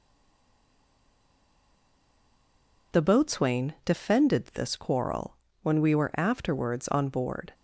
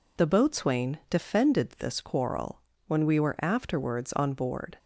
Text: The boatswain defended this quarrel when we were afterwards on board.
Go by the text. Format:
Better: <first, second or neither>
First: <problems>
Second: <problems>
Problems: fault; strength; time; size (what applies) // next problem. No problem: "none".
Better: second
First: stays silent before the first word; strong; until 2.9 s; 2.9 s long // pauses between "quarrel" and "when"; slight; at 5.3 s; 0.26 s long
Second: pauses between "quarrel" and "when"; slight; at 2.6 s; 0.26 s long